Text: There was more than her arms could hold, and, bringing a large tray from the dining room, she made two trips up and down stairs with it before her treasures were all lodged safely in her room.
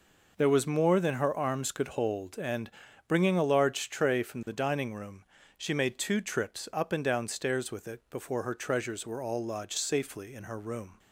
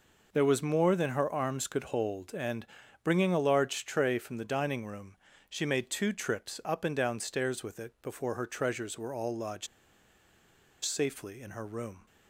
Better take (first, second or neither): first